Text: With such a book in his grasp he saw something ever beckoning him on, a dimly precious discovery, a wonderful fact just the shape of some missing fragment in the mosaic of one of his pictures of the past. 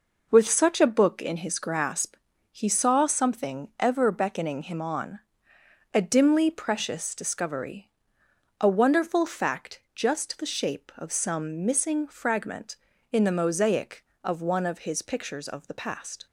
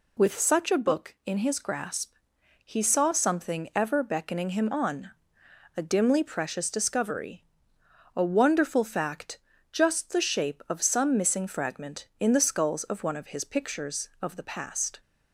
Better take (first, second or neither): first